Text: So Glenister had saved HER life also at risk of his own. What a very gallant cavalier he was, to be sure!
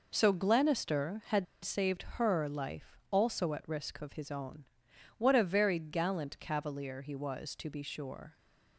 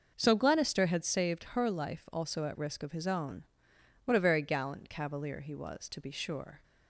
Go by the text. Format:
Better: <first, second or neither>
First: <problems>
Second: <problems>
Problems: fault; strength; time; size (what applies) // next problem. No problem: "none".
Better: second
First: pauses between "had" and "saved"; slight; at 1.4 s; 0.17 s long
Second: none